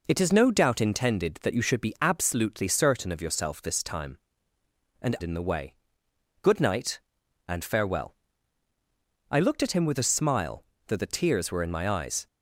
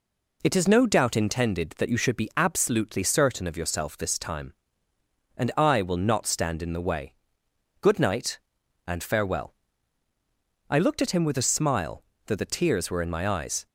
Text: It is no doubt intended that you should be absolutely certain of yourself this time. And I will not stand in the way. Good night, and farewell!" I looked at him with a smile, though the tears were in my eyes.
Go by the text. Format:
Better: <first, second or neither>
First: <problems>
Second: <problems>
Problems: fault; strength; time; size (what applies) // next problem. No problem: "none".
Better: second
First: skips "I will not stand"; at 5.1 s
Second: none